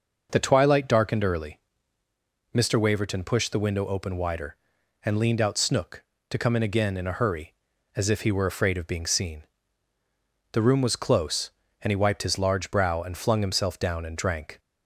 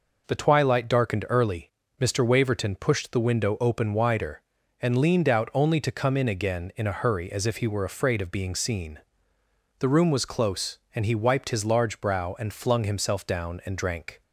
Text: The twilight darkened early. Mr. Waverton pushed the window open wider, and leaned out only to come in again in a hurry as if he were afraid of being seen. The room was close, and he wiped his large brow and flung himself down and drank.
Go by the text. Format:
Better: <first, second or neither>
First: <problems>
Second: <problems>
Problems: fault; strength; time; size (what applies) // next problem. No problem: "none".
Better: second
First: says "snook" for "only"; at 5.5 s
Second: none